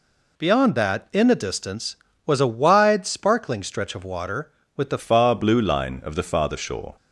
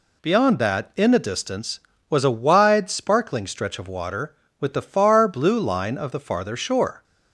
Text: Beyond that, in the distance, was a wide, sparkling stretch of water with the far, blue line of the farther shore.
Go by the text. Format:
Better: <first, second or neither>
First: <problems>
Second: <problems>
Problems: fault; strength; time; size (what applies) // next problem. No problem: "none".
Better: second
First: changes voice at "far"; from 4.9 s on; 2.0 s long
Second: none